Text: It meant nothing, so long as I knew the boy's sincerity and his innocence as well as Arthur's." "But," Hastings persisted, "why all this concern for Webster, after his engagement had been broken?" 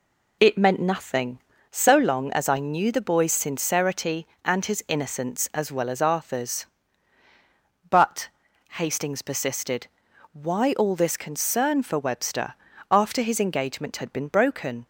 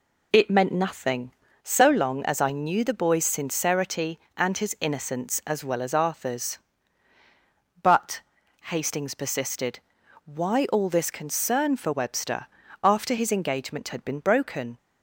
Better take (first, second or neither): neither